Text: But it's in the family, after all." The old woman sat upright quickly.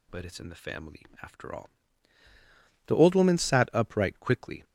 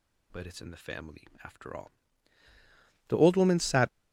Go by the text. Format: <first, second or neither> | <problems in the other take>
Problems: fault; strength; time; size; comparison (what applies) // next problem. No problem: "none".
first | stops before "upright quickly"; at 3.8 s